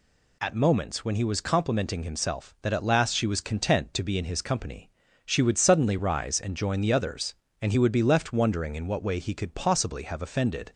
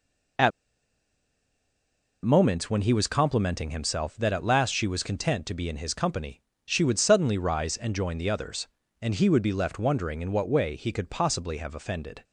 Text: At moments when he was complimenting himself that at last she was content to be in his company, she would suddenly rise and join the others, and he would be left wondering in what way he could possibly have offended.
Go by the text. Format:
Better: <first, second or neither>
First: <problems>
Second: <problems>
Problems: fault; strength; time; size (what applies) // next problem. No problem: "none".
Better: first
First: none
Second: pauses between "At" and "moments"; strong; at 0.5 s; 1.7 s long